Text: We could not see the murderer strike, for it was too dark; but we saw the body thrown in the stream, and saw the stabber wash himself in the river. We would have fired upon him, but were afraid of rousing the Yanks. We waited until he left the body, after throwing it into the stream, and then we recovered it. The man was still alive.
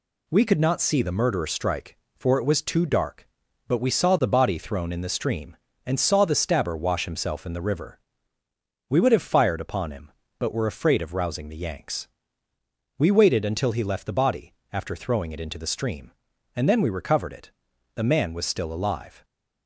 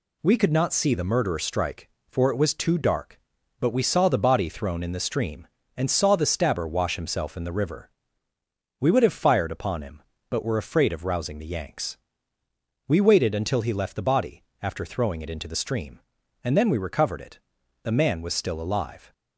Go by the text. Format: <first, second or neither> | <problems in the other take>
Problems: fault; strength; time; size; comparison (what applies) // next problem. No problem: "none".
neither | none